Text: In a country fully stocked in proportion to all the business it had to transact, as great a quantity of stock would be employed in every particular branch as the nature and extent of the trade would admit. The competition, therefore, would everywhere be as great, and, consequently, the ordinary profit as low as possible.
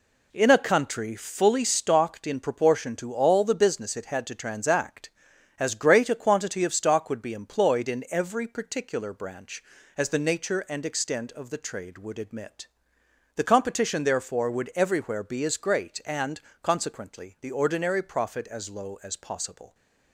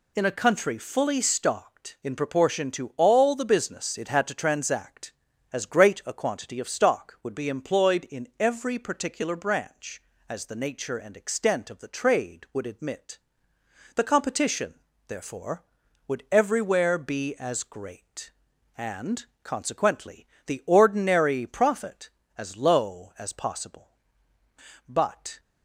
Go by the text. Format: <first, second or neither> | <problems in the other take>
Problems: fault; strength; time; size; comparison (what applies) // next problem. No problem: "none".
first | goes on to say "But"; from 24.8 s on; 0.52 s long